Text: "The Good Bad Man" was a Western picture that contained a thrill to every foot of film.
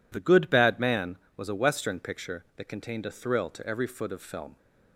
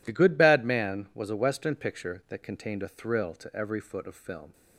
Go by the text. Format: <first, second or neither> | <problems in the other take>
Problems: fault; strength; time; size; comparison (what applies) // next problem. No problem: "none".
neither | none